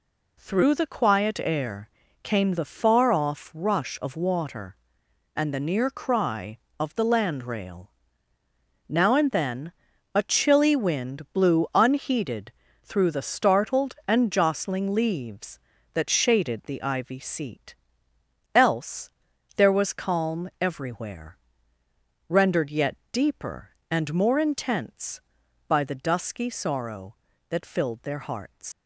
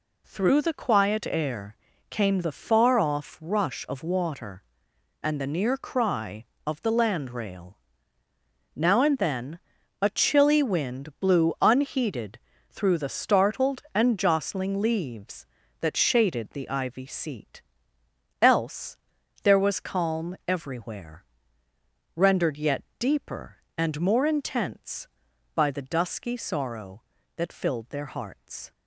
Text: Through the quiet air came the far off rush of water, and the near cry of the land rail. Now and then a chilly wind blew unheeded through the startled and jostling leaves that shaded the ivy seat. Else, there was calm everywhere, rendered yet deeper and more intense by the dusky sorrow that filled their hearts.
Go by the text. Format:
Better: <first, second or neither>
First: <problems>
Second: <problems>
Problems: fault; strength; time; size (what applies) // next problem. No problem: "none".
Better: second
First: pauses between "air" and "came"; slight; at 1.9 s; 0.32 s long // pauses between "then" and "a"; at 9.7 s; 0.42 s long // pauses between "unheeded" and "through"; slight; at 12.5 s; 0.32 s long // pauses between "yet" and "deeper"; slight; at 22.9 s; 0.16 s long // leaves "hearts" unfinished; at 28.7 s; 125 ms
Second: pauses between "air" and "came"; slight; at 1.7 s; 0.32 s long // pauses between "then" and "a"; at 9.5 s; 0.42 s long // pauses between "unheeded" and "through"; slight; at 12.3 s; 0.32 s long // pauses between "yet" and "deeper"; slight; at 22.8 s; 0.16 s long